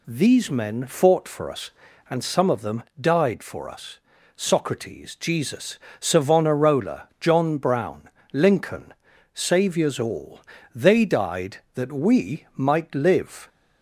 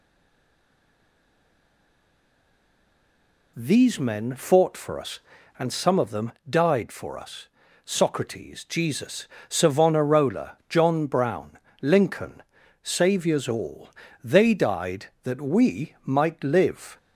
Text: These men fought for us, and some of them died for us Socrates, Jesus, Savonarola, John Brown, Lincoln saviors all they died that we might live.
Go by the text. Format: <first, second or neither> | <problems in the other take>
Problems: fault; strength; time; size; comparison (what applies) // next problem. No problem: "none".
first | stays silent before the first word; strong; until 3.5 s; 3.5 s long // pauses between "them" and "died"; slight; at 6.3 s; 0.18 s long; slight in the first // pauses between "us" and "Socrates"; slight; at 7.4 s; 0.36 s long; slight in the first // pauses between "Lincoln" and "saviors"; at 12.4 s; 0.40 s long; also in the first // pauses between "all" and "they"; slight; at 13.9 s; 0.32 s long; slight in the first